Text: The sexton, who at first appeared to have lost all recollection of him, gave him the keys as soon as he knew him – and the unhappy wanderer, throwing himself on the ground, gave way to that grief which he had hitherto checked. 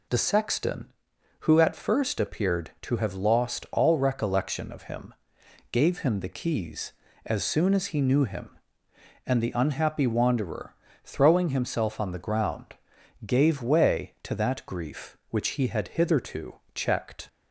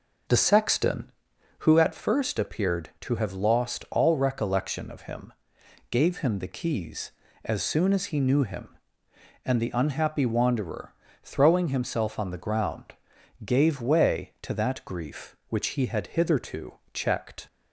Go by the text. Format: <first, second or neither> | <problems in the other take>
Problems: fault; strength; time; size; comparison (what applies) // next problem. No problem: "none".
first | starts louder than the rest; noticeable; until 1.8 s; 5 dB // pauses between "hitherto" and "checked"; slight; at 16.7 s; 0.16 s long; slight in the first